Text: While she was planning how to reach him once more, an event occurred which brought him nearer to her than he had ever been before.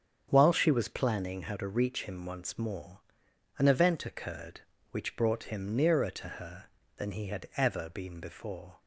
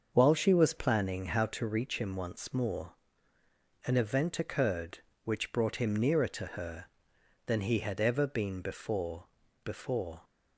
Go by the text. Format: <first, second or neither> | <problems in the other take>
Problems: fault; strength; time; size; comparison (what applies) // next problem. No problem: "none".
first | starts louder than the rest; until 1.1 s; 6.5 dB; strong in the first // says "before" twice; at 9.6 s